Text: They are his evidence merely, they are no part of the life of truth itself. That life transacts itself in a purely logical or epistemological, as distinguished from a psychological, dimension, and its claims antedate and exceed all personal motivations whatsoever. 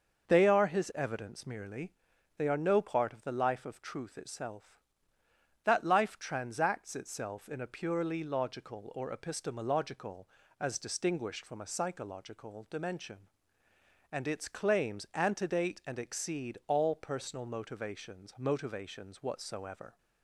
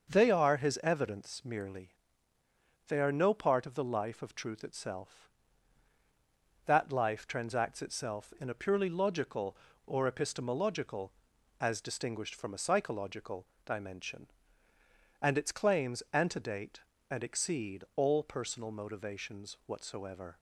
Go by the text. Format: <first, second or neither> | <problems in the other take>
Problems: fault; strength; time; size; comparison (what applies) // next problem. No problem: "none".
second | starts louder than the rest; until 1.3 s; 6 dB; also in the second // says "motivations" twice; at 18.3 s